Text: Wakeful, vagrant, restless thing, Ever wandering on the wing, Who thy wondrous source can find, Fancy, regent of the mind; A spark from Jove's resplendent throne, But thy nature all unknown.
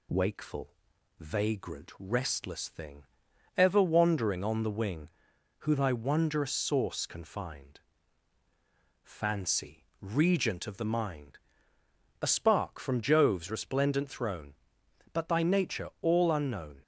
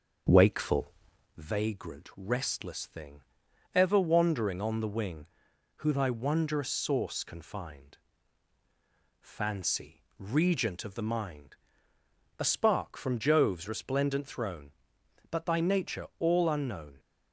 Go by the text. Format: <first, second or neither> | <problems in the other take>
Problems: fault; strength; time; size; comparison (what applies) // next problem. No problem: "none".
first | starts louder than the rest; until 1.4 s; 6.5 dB